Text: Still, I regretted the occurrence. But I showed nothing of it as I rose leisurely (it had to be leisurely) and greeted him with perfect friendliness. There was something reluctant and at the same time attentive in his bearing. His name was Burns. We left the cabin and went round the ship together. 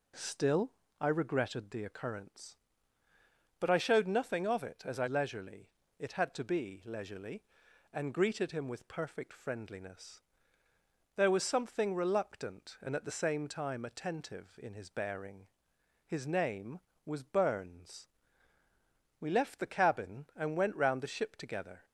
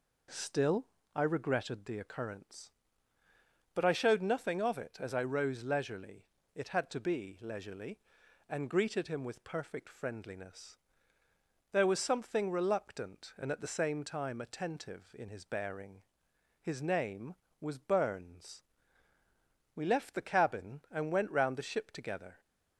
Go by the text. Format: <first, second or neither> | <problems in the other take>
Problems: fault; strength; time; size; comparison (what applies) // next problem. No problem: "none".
second | skips "rose"; at 5.0 s